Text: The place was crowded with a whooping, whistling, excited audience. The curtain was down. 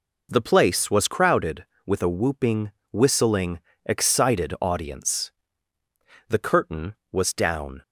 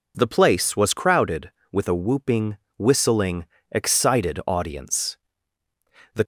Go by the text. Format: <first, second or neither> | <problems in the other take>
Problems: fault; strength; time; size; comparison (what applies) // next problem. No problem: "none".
first | stops before "curtain was down"; at 6.2 s